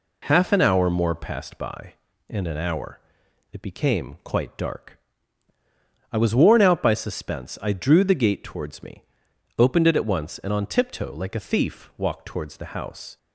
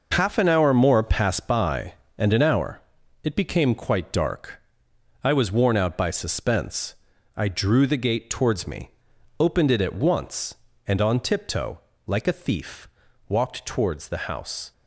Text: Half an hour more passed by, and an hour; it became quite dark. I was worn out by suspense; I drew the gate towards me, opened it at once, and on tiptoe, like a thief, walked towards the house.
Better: neither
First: none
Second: none

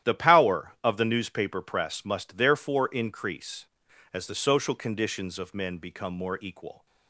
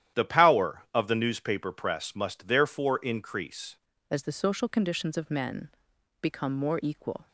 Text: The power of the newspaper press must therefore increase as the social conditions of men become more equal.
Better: first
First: starts louder than the rest; strong; until 1.1 s; 11.5 dB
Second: starts louder than the rest; strong; until 1.2 s; 11 dB // changes voice at "as"; from 4.0 s on; 3.2 s long // pauses between "men" and "become"; noticeable; at 5.6 s; 0.52 s long

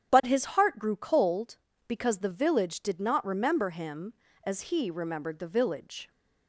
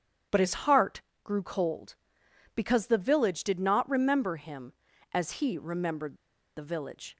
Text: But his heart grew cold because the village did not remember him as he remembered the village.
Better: first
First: starts louder than the rest; strong; until 1.1 s; 9.5 dB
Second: starts louder than the rest; strong; until 1.5 s; 9 dB // pauses between "heart" and "grew"; slight; at 1.0 s; 0.22 s long // pauses between "remembered" and "the"; at 6.1 s; 0.41 s long

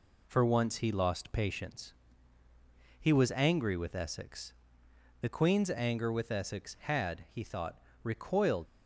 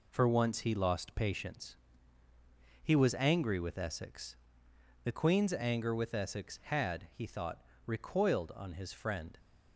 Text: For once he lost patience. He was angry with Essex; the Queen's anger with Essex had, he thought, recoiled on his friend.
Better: second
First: stops before "on his friend"; at 8.6 s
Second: none

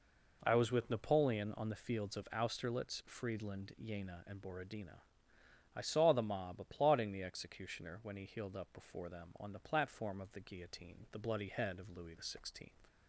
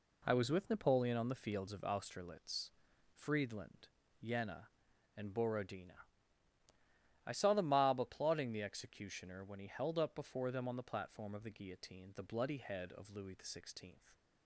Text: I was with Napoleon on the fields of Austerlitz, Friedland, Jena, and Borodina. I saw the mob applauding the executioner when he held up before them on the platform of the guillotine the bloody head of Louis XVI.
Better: second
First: says "healed" for "held"; at 8.2 s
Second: none

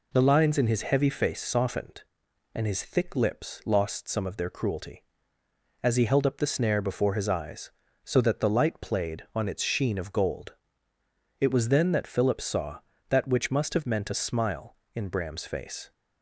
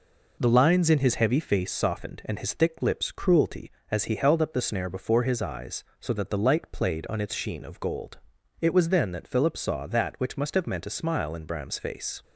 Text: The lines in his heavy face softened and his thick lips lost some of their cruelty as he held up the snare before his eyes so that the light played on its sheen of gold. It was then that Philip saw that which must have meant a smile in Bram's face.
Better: first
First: none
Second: skips "lost some of their"; at 3.1 s

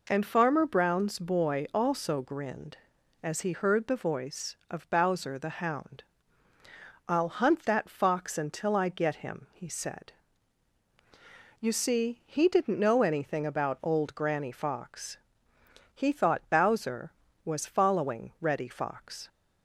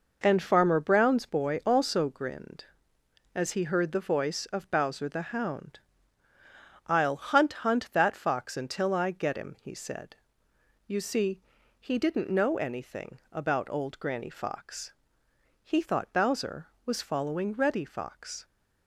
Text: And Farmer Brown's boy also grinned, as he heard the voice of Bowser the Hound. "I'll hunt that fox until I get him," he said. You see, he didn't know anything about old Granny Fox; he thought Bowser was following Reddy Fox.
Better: first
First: none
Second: says "hunt" twice; at 7.6 s

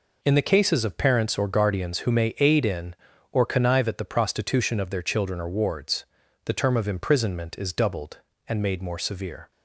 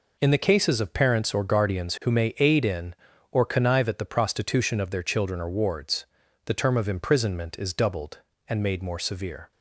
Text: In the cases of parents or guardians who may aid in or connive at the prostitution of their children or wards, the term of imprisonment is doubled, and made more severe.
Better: neither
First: none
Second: none

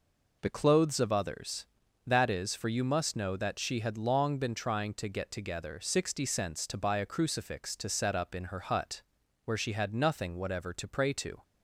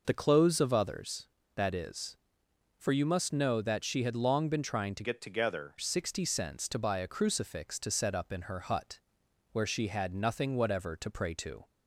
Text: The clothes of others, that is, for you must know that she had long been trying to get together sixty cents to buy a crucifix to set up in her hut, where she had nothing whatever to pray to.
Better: first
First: none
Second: changes voice from "get" to "together"; from 5.0 to 5.7 s; 0.7 s long

